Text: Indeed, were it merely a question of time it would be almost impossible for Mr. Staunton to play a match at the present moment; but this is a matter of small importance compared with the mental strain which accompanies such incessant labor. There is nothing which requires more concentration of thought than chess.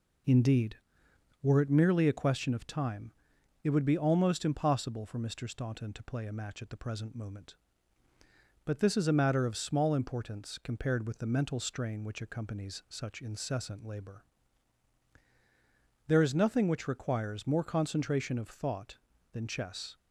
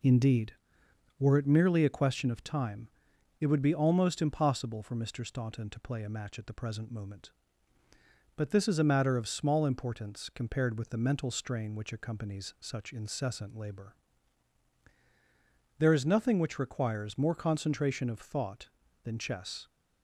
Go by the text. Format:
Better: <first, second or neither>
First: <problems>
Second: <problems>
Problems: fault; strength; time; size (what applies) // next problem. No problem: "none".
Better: neither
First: pauses between "time" and "it"; noticeable; at 3.1 s; 0.52 s long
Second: pauses between "time" and "it"; noticeable; at 2.8 s; 0.52 s long